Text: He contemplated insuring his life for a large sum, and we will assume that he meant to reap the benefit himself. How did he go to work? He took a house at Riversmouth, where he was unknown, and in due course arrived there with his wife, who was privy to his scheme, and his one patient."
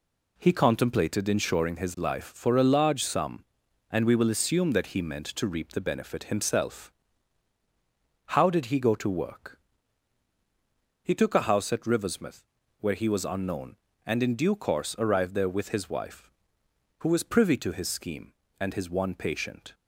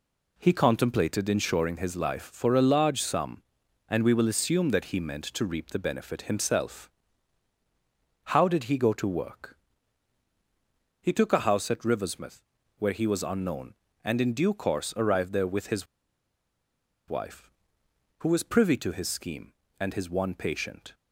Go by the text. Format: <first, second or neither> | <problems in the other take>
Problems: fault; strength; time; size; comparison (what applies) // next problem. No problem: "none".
first | pauses between "his" and "wife"; at 15.8 s; 1.2 s long